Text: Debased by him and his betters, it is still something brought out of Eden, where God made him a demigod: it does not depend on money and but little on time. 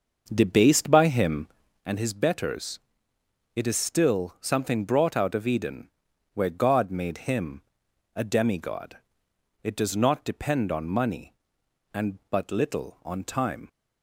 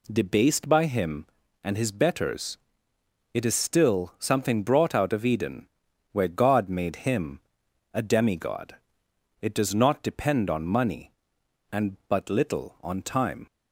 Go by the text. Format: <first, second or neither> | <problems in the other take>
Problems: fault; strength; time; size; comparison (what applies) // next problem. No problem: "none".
second | starts louder than the rest; until 2.0 s; 6 dB // pauses between "him" and "a"; noticeable; at 7.6 s; 0.54 s long; noticeable in the second